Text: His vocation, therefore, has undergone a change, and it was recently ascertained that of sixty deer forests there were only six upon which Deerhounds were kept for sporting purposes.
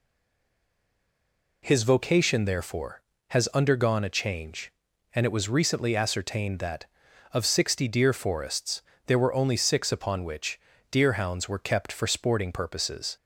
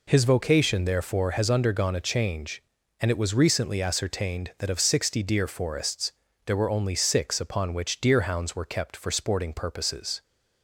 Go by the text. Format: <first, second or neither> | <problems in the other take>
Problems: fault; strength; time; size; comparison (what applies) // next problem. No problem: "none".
second | stays silent before the first word; noticeable; until 1.6 s; 1.6 s long // pauses between "forests" and "there"; slight; at 8.8 s; 0.24 s long; slight in the second // pauses between "which" and "Deerhounds"; slight; at 10.5 s; 0.30 s long